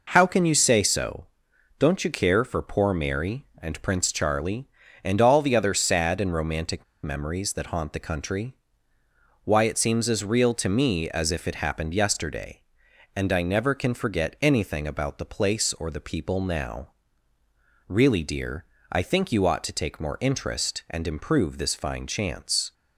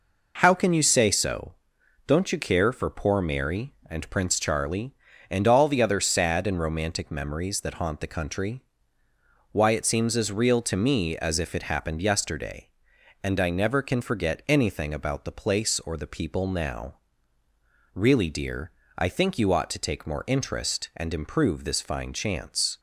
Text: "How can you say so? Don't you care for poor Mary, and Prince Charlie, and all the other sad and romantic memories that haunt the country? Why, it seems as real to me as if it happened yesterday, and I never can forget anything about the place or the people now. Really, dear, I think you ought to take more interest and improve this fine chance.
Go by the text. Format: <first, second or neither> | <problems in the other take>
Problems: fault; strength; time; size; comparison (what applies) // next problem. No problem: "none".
second | pauses between "romantic" and "memories"; slight; at 6.8 s; 0.20 s long